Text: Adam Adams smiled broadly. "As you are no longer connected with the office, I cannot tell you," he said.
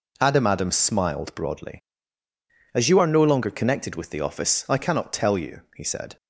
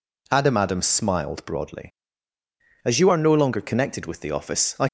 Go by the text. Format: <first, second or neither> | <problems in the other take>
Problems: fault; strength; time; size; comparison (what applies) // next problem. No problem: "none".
first | stops before "cannot tell you he said"; at 4.8 s